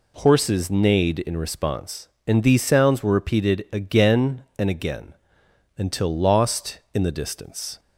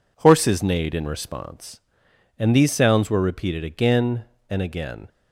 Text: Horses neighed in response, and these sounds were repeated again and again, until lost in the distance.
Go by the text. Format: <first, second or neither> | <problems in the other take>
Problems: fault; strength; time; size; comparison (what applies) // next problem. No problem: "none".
first | stops before "until lost in the distance"; at 5.0 s